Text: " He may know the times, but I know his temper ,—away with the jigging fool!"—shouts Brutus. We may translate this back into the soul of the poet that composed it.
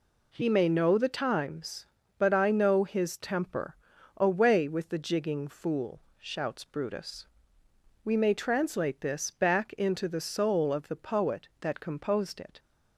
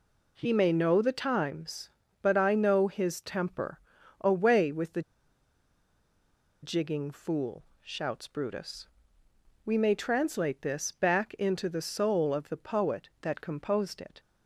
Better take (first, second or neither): first